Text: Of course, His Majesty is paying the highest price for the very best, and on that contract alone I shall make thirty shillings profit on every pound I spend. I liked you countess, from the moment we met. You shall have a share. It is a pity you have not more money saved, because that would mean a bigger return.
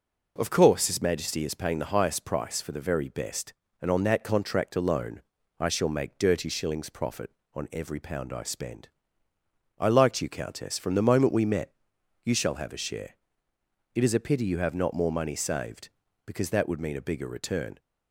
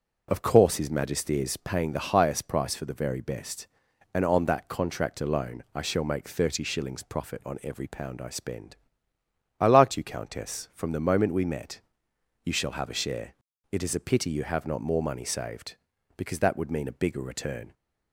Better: second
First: pauses between "alone" and "I"; slight; at 5.2 s; 0.36 s long // says "dirty" for "thirty"; at 6.1 s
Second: none

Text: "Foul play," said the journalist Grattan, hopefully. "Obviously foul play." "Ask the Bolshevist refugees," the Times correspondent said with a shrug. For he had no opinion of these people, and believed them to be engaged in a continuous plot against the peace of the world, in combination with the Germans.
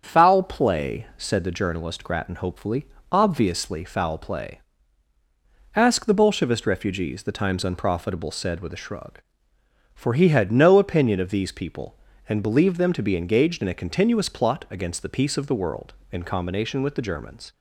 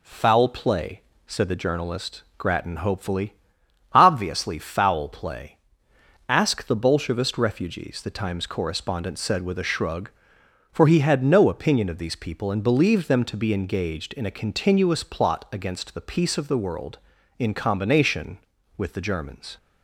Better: second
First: starts louder than the rest; strong; until 1.0 s; 7.5 dB // says "unprofitable" for "correspondent"; at 7.6 s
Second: none

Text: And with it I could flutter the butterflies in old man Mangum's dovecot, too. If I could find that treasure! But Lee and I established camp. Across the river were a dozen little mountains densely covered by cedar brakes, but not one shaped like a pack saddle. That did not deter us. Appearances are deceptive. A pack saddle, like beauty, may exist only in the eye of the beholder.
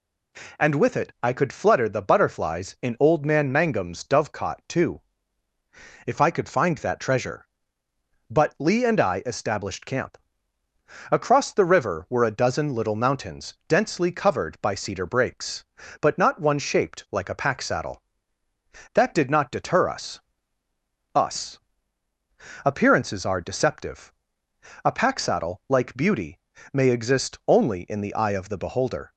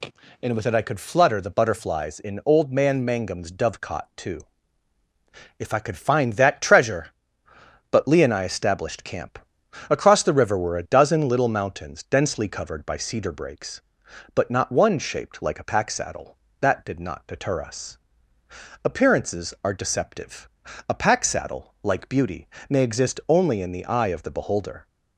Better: second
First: says "us" twice; at 21.1 s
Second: none

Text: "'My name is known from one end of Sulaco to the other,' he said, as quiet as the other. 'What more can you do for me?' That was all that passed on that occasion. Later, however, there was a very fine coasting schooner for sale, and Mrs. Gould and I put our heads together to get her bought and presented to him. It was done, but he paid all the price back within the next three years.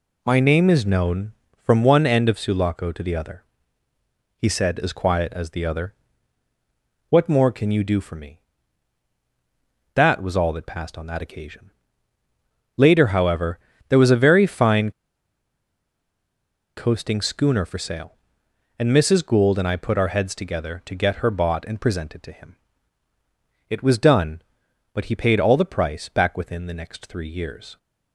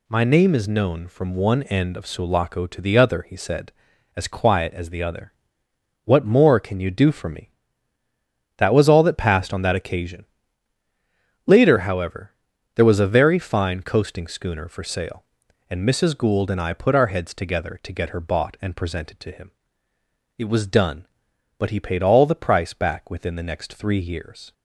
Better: second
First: pauses between "fine" and "coasting"; strong; at 14.9 s; 1.8 s long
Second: none

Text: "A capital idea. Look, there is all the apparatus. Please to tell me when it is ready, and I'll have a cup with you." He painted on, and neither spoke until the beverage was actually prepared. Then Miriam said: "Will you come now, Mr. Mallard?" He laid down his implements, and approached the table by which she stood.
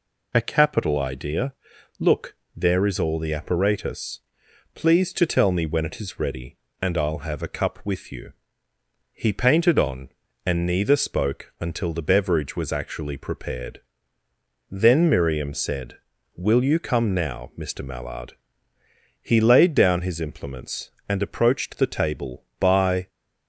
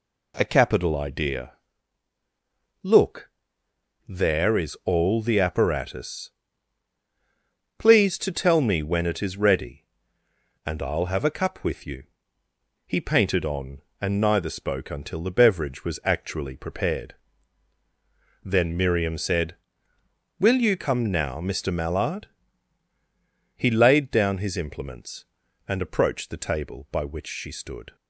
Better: second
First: stops before "which she stood"; at 23.0 s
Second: none

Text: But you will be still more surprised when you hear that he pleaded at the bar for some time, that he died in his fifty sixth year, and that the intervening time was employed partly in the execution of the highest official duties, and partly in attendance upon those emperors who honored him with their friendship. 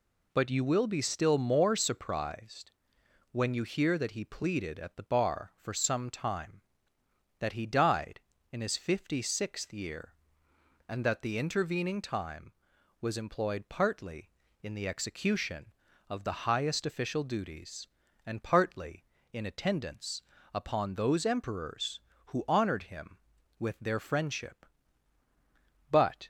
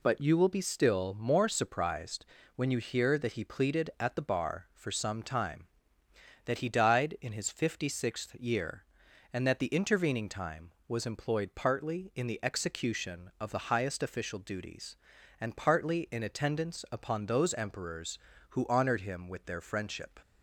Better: second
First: pauses between "surprised" and "when"; noticeable; at 2.7 s; 0.60 s long // pauses between "attendance" and "upon"; slight; at 20.2 s; 0.32 s long // goes on to say "But"; slight; from 25.8 s on; 0.38 s long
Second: pauses between "surprised" and "when"; slight; at 2.2 s; 0.32 s long

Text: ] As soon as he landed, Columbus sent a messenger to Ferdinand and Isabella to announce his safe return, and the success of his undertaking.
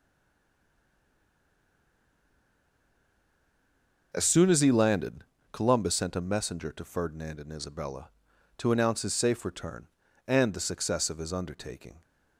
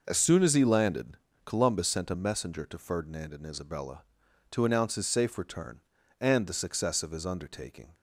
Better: second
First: stays silent before the first word; strong; until 4.1 s; 4.1 s long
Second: none

